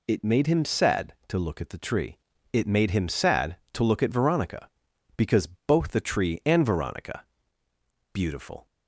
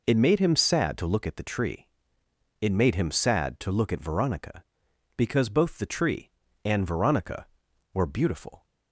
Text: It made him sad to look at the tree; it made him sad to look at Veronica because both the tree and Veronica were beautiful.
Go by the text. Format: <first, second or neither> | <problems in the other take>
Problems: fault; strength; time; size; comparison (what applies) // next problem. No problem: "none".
second | pauses between "because" and "both"; slight; at 5.4 s; 0.18 s long // skips "were"; at 7.6 s